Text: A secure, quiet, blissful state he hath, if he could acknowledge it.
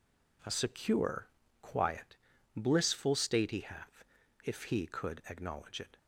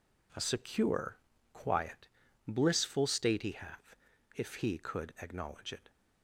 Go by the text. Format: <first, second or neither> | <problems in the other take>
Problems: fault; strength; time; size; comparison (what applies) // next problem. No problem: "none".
neither | none